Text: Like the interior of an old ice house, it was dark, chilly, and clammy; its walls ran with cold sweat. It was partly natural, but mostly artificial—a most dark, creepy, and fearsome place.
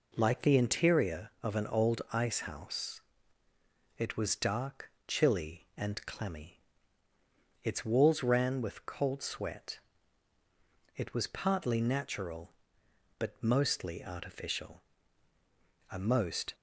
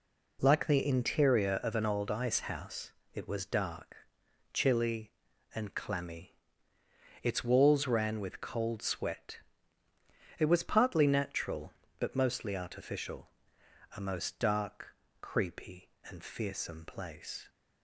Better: second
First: stops before "dark creepy and fearsome place"; at 16.5 s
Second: none

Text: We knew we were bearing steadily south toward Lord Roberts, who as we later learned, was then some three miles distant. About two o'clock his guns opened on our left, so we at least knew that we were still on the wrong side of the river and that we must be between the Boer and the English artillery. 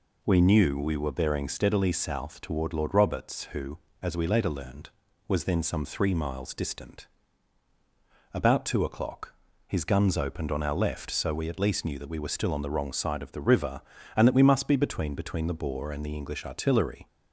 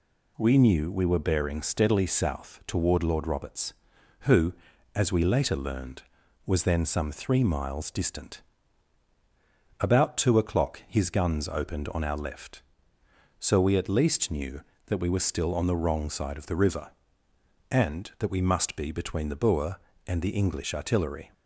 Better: second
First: pauses between "o'clock" and "his"; slight; at 9.3 s; 0.34 s long // says "between" twice; at 15.1 s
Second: none

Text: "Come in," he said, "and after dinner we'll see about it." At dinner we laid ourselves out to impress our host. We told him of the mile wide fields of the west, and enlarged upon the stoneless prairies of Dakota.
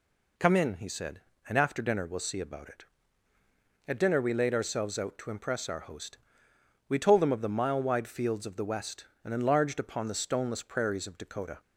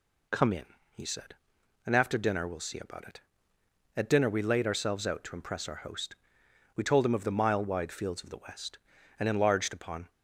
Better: first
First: none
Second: stops before "the stoneless prairies of Dakota"; at 10.0 s

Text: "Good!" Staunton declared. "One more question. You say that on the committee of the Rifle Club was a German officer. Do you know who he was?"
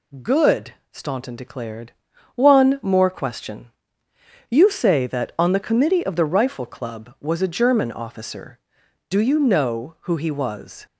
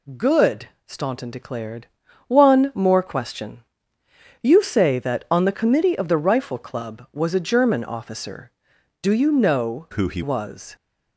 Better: first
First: none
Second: changes voice from "who" to "he"; from 9.9 to 10.2 s; 0.3 s long

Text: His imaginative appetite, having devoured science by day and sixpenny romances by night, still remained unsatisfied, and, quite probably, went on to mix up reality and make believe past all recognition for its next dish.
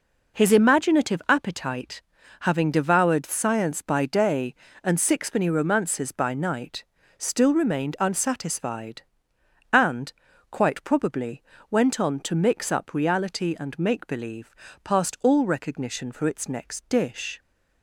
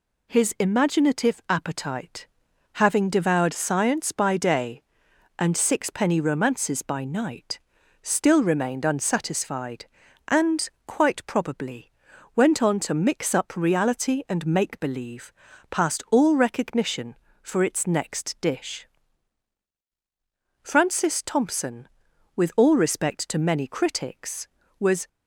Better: first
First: pauses between "believe" and "past"; slight; at 14.5 s; 0.30 s long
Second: pauses between "believe" and "past"; at 15.3 s; 0.38 s long // goes on to say "Francis Thompson with all respect to many critics was"; strong; from 20.6 s on; 4.4 s long

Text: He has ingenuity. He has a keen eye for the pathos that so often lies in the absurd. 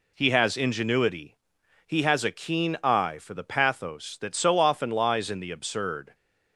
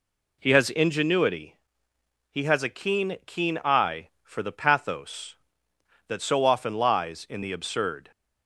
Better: first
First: none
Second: says "keen" twice; at 3.2 s

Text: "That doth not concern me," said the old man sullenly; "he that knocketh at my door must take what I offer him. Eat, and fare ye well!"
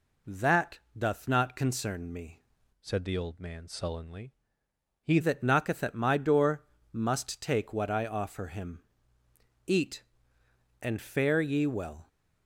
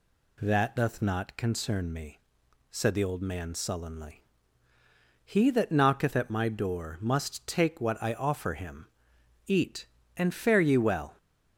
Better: second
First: pauses between "That" and "doth"; slight; at 0.7 s; 0.18 s long // changes voice from "said" to "he"; from 2.8 to 5.1 s; 2.3 s long // pauses between "door" and "must"; slight; at 6.6 s; 0.30 s long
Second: none

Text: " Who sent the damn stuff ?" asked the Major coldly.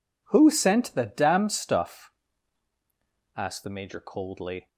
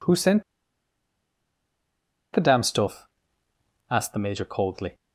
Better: first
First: none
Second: pauses between "sent" and "the"; strong; at 0.4 s; 1.9 s long

